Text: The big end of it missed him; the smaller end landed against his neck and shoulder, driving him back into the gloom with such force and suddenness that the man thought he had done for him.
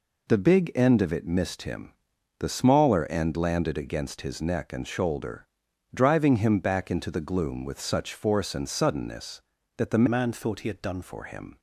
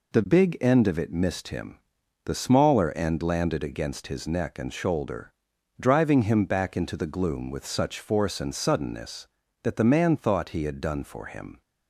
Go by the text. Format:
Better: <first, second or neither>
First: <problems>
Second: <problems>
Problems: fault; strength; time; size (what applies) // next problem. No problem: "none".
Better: second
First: changes voice from "man" to "done"; from 10.0 to 11.0 s; 1.0 s long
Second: none